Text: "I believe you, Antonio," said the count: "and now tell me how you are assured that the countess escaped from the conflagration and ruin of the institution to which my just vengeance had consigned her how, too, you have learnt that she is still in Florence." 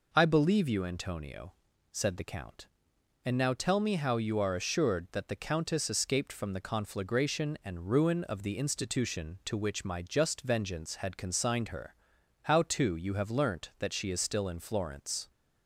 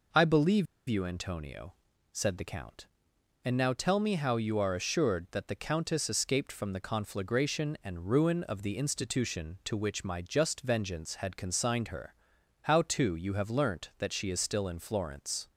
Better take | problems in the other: first | pauses between "believe" and "you"; slight; at 0.6 s; 0.22 s long // pauses between "her" and "how"; noticeable; at 12.1 s; 0.48 s long; noticeable in the first

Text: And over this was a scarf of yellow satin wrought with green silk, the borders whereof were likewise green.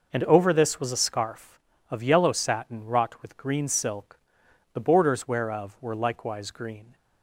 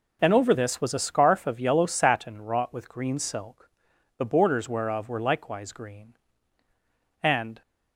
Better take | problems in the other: first | goes on to say "And"; slight; from 7.2 s on; 0.38 s long

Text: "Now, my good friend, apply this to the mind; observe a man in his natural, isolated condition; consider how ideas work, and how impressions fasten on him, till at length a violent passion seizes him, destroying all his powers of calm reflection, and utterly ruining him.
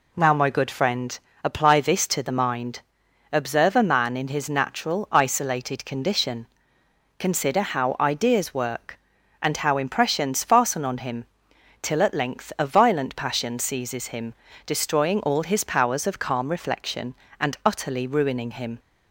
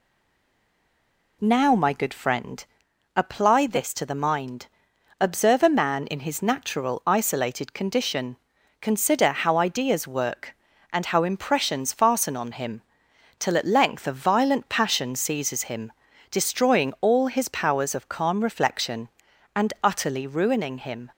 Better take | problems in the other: first | stays silent before the first word; noticeable; until 1.4 s; 1.4 s long

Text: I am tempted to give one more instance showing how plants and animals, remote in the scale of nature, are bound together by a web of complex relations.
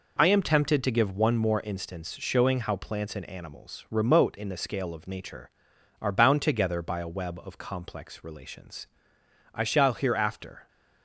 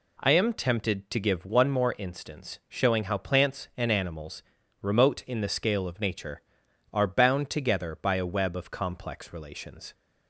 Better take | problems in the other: second | goes on to say "I shall hereafter"; noticeable; from 9.5 s on; 1.1 s long

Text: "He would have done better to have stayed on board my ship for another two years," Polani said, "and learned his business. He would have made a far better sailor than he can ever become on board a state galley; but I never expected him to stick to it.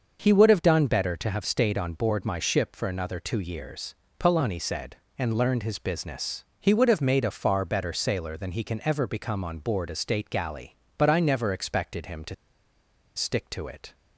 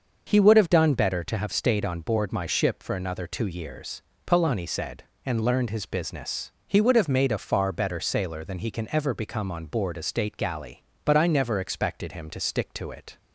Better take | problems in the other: second | starts louder than the rest; until 1.2 s; 6.5 dB; also in the second // pauses between "to" and "stick"; noticeable; at 12.3 s; 0.81 s long

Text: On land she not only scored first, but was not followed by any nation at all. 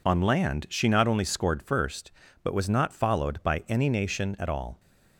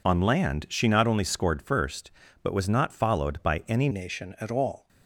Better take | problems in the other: first | changes voice at "nation"; from 3.9 s on; 0.9 s long

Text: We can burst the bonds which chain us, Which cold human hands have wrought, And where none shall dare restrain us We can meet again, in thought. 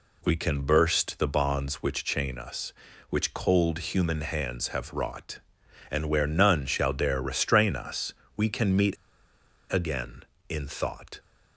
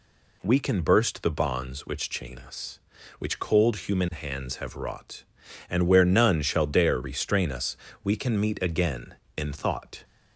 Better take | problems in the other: second | pauses between "us" and "We"; slight; at 8.1 s; 0.24 s long; slight in the second // pauses between "meet" and "again"; noticeable; at 8.9 s; 0.76 s long

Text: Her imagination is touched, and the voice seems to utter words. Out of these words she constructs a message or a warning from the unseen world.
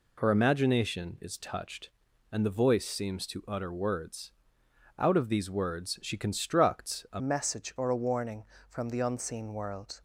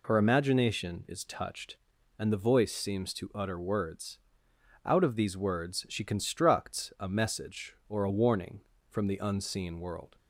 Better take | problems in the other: second | changes voice at "message"; from 7.1 s on; 2.9 s long

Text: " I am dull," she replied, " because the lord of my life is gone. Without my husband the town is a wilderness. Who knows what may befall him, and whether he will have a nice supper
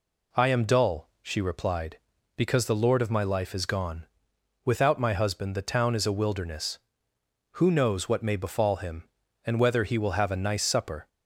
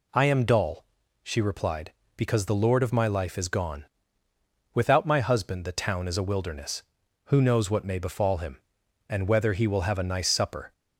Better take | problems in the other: neither | none

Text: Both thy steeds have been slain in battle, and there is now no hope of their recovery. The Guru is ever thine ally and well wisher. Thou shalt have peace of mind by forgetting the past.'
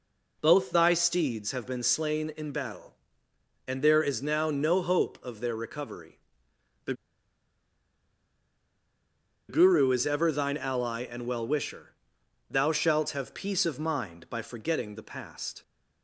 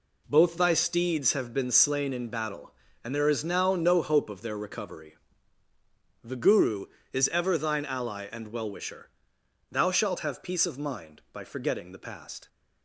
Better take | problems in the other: second | pauses between "The" and "Guru"; strong; at 6.9 s; 2.5 s long

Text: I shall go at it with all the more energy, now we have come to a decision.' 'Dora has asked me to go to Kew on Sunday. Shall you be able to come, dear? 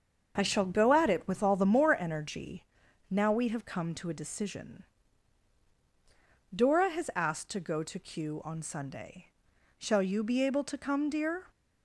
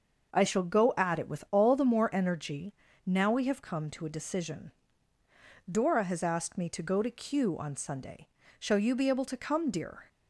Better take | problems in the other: second | starts louder than the rest; until 1.3 s; 6.5 dB; also in the second // skips "me"; at 7.4 s

